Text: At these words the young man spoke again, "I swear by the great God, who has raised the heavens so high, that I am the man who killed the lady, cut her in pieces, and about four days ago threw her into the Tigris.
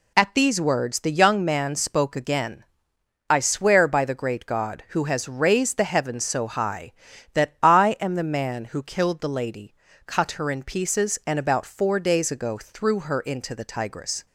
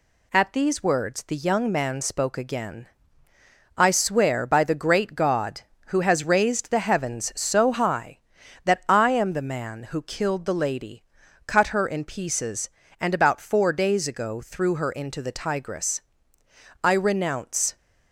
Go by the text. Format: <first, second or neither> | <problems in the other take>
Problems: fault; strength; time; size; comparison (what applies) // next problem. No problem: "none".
first | goes on to say "I renounce"; noticeable; from 16.8 s on; 0.94 s long